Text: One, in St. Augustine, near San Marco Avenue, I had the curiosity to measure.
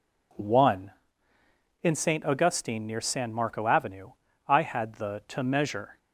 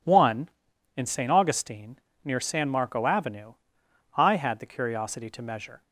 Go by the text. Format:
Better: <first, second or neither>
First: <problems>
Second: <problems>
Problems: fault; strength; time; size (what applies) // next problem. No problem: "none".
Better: second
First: skips "curiosity"; at 5.2 s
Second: none